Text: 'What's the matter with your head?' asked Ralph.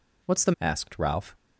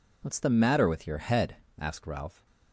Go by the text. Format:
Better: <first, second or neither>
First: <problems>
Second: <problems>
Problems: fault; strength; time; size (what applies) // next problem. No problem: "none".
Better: second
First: skips "matter with your head"; at 0.5 s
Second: none